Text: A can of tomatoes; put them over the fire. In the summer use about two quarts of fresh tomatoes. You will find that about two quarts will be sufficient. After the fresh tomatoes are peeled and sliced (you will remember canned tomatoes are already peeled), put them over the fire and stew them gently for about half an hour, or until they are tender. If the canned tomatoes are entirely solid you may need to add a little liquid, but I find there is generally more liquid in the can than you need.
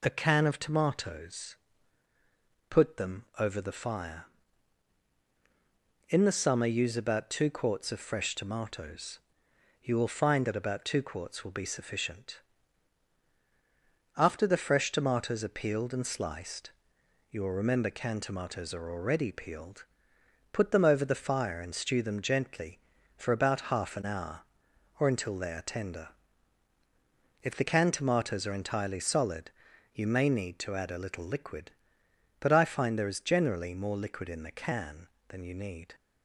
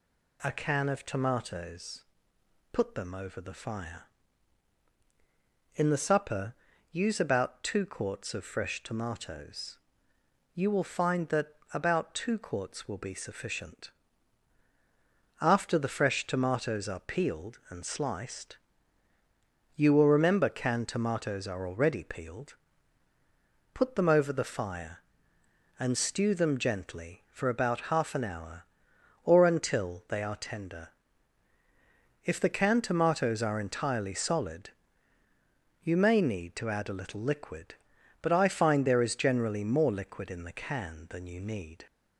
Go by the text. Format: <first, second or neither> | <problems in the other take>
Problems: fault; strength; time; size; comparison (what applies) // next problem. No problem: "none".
first | says "supper" for "summer"; at 5.9 s // pauses between "that" and "about"; slight; at 11.4 s; 0.26 s long // pauses between "solid" and "you"; at 34.7 s; 1.1 s long; also in the first